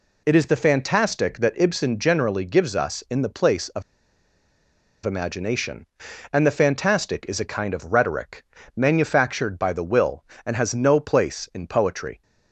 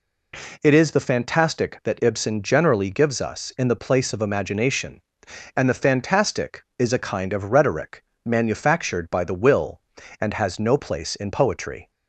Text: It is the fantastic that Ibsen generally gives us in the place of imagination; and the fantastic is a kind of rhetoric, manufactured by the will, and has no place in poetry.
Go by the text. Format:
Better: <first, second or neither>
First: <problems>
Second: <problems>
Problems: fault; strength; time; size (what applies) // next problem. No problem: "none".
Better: second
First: pauses between "of" and "imagination"; at 3.8 s; 1.2 s long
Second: none